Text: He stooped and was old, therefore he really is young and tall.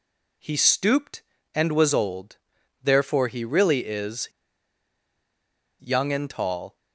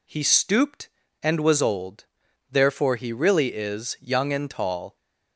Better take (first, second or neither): second